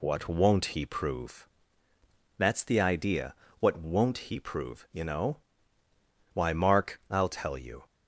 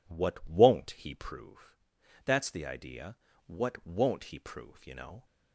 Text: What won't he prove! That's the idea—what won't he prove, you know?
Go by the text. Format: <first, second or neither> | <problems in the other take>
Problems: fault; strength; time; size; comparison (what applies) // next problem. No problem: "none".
second | goes on to say "Why Mark I'll tell you"; from 6.3 s on; 1.5 s long